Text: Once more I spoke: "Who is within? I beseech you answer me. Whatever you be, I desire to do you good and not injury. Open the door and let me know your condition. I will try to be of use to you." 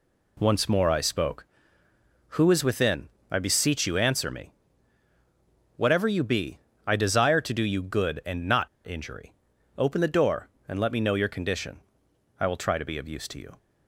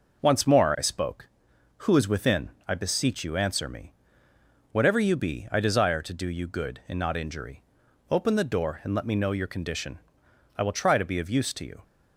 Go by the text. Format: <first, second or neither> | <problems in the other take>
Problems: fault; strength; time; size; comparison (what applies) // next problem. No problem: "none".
second | pauses between "not" and "injury"; slight; at 8.6 s; 0.17 s long